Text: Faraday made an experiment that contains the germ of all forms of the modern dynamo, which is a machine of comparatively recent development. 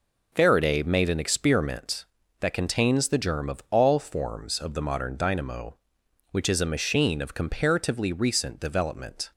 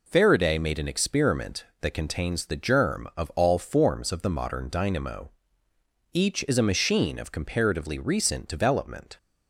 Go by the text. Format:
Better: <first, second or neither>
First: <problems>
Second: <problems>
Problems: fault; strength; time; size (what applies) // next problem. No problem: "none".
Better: first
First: none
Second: says "each" for "which"; at 6.1 s